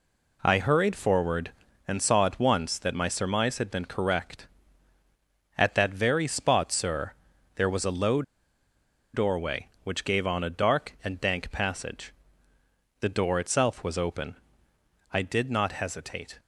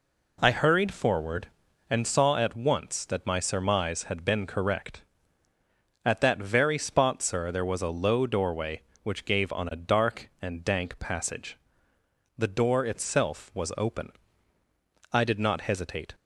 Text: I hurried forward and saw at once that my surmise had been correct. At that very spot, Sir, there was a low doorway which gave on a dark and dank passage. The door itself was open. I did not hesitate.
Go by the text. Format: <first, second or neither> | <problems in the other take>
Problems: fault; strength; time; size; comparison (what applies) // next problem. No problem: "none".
second | pauses between "low" and "doorway"; noticeable; at 8.2 s; 0.91 s long